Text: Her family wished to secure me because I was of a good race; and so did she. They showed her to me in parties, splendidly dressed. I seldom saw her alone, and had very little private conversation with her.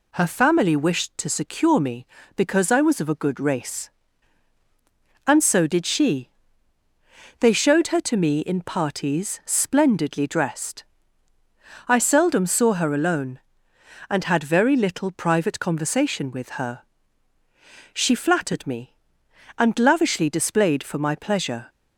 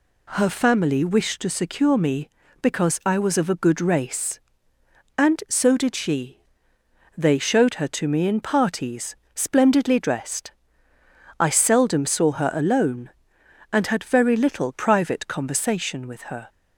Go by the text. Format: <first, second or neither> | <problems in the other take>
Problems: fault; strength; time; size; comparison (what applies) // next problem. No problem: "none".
second | goes on to say "She flattered me and lavishly displayed for my pleasure"; strong; from 17.9 s on; 3.7 s long